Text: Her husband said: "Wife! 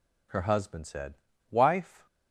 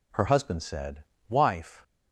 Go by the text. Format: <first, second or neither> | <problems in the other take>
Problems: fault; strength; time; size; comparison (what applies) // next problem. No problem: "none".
neither | none